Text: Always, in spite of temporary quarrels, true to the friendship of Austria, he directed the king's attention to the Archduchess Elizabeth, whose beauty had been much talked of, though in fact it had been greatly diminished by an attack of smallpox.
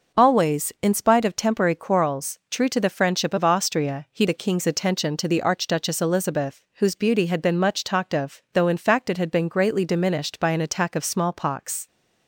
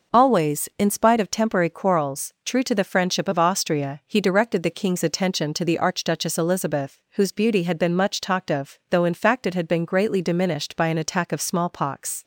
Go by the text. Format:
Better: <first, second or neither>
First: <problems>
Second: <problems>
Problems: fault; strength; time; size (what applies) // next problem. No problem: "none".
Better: second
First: skips "directed"; at 4.2 s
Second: none